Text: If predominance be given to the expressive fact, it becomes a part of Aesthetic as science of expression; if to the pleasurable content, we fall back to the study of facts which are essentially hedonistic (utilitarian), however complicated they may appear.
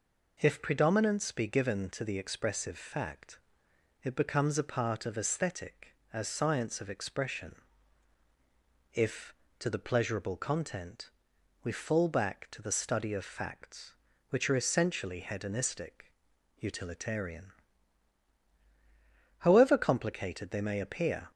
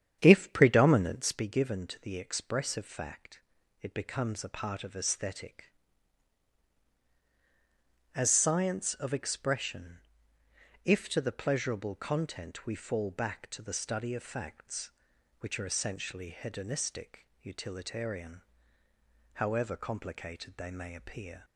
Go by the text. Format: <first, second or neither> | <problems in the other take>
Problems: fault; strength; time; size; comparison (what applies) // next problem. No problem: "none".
first | starts louder than the rest; strong; until 1.5 s; 9 dB